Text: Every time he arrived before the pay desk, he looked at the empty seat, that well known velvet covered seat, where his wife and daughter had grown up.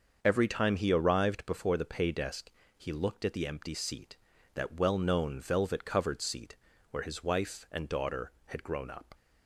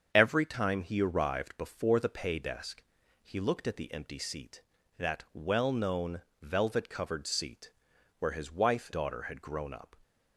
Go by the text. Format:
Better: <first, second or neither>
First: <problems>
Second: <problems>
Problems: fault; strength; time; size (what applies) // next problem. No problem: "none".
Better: first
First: starts louder than the rest; until 1.2 s; 6.5 dB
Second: starts louder than the rest; until 1.1 s; 7 dB // pauses between "known" and "velvet"; slight; at 6.2 s; 0.20 s long // skips "and"; at 8.9 s